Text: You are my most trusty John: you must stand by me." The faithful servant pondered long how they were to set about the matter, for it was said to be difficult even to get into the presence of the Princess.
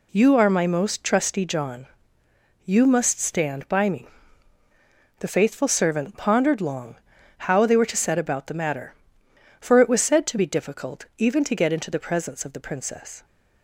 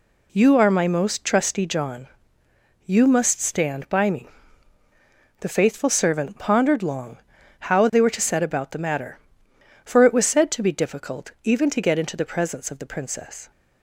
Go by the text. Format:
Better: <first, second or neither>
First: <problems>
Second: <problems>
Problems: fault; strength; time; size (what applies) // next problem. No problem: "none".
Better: neither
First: pauses between "long" and "how"; at 6.9 s; 0.44 s long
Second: pauses between "long" and "how"; at 7.1 s; 0.44 s long